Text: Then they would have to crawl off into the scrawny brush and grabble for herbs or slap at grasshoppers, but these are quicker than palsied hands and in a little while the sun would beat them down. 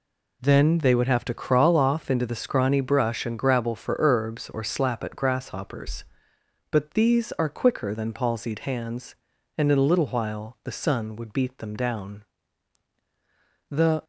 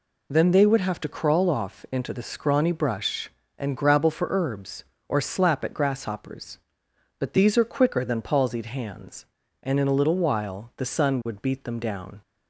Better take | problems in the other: second | goes on to say "The"; slight; from 13.6 s on; 0.34 s long

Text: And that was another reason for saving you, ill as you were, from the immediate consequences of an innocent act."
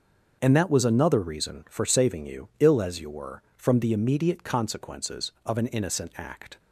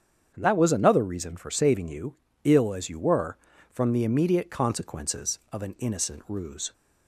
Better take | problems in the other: first | starts louder than the rest; strong; until 1.3 s; 7.5 dB; also in the first // says "ruse" for "act"; at 6.2 s

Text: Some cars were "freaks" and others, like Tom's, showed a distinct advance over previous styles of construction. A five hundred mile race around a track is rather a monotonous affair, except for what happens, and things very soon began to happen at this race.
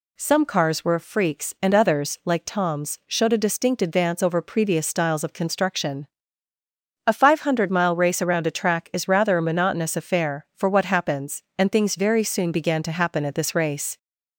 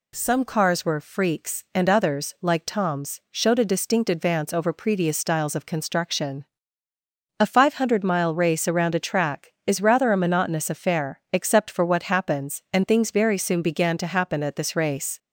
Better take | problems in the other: second | skips "except"; at 10.5 s

